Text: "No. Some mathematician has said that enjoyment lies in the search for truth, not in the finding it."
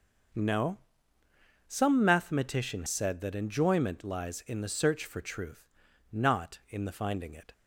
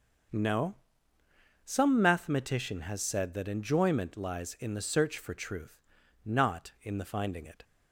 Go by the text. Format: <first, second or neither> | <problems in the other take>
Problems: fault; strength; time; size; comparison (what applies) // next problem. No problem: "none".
second | starts louder than the rest; until 2.2 s; 6 dB; also in the second // skips "has"; at 2.8 s